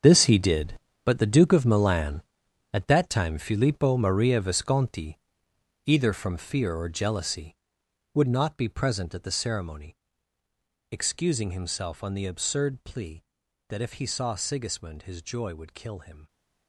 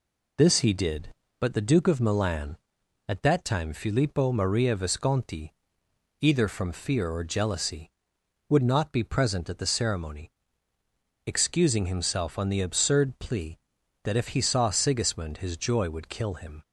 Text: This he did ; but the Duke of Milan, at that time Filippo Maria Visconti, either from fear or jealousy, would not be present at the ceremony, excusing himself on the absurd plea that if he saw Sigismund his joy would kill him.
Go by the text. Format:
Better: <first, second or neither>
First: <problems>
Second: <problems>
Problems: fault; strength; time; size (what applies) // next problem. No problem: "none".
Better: second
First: gets quieter; strong; throughout; 13 dB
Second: none